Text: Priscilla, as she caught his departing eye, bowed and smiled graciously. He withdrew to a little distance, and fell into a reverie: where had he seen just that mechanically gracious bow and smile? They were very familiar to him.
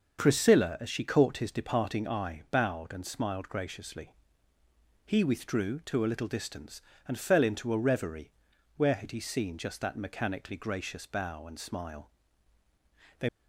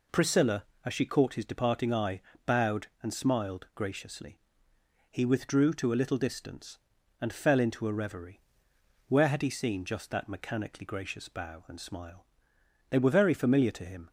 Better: second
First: starts louder than the rest; until 1.2 s; 7 dB // stops before "were very familiar to him"; at 13.2 s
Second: none

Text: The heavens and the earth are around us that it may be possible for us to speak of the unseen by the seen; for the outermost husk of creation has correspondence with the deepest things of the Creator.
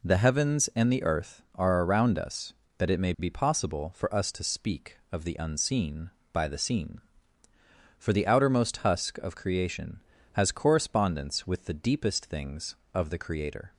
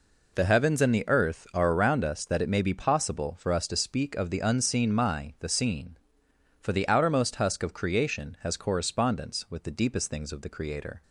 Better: first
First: none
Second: says "my" for "by"; at 4.9 s

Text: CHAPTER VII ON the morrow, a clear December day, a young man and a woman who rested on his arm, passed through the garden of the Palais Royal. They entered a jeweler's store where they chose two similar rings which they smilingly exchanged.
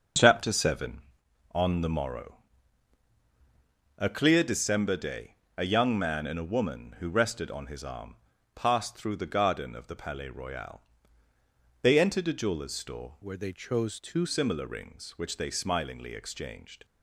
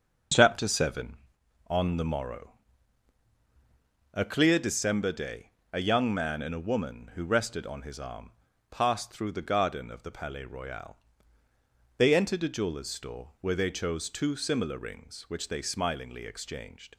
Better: second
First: changes voice from "where" to "two"; from 13.2 to 14.2 s; 1.0 s long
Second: none

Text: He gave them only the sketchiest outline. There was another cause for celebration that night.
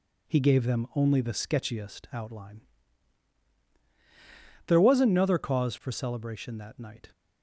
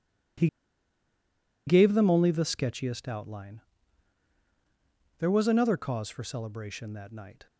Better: first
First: none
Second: pauses between "He" and "gave"; at 0.4 s; 1.2 s long

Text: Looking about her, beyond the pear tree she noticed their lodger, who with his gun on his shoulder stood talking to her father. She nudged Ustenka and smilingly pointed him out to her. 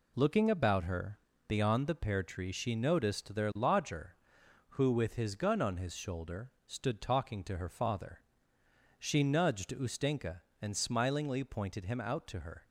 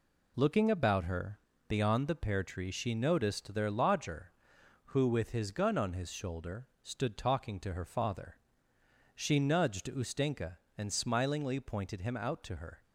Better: neither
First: pauses between "shoulder" and "stood"; slight; at 6.4 s; 0.16 s long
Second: pauses between "shoulder" and "stood"; slight; at 6.6 s; 0.16 s long

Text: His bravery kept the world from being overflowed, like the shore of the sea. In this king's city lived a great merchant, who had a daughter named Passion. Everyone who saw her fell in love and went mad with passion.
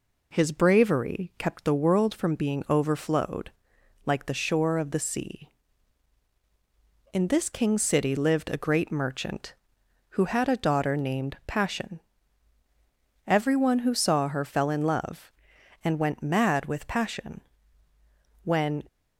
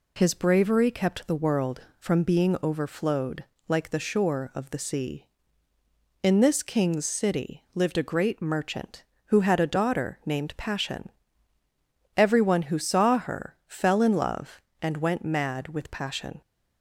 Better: second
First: goes on to say "When"; slight; from 18.4 s on; 0.40 s long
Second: none

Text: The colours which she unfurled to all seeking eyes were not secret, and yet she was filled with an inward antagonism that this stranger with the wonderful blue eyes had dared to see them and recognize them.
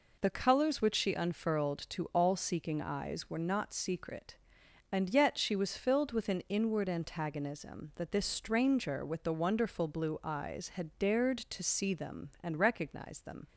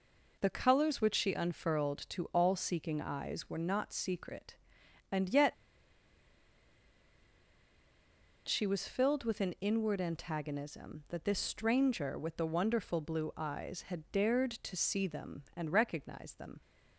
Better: first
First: none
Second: pauses between "yet" and "she"; strong; at 5.5 s; 2.9 s long

